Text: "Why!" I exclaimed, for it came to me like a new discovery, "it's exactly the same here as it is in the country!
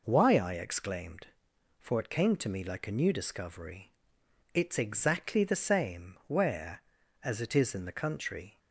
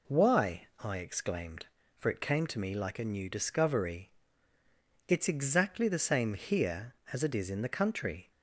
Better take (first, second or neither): second